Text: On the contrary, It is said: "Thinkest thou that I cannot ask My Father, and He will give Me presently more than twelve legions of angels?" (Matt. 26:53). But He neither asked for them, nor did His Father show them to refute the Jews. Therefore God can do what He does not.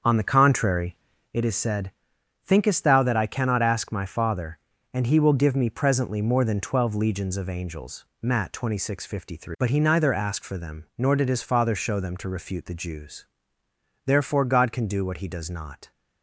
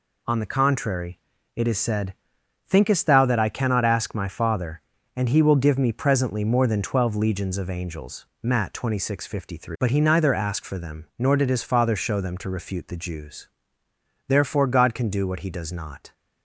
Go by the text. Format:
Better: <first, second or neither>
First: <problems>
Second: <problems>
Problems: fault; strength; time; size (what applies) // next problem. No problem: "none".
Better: second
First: starts louder than the rest; strong; until 1.4 s; 7 dB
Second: none